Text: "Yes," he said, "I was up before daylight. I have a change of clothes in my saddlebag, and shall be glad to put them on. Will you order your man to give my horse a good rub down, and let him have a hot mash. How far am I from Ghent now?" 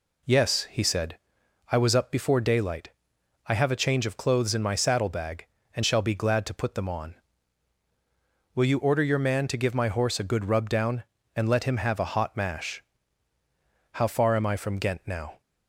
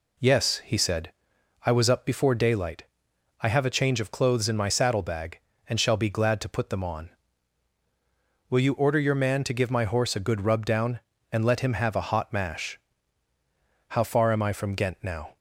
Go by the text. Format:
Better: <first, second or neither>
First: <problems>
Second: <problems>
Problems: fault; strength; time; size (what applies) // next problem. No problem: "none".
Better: neither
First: none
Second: none